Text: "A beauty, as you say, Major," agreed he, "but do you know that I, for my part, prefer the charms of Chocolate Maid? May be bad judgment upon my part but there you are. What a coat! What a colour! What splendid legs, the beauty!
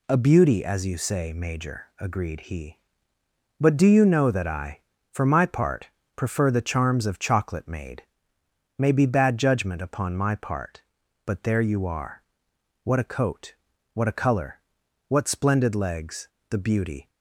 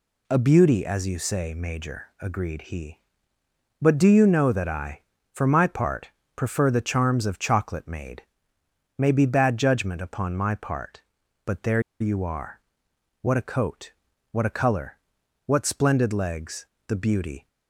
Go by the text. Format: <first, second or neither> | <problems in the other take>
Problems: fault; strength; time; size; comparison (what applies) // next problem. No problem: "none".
first | pauses between "there" and "you"; slight; at 11.8 s; 0.19 s long